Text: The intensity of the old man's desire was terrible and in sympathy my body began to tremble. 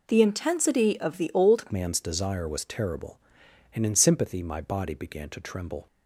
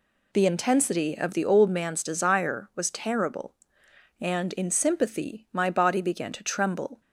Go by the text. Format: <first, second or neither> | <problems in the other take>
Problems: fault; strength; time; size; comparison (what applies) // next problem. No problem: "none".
second | changes voice at "man's"; from 1.7 s on; 4.1 s long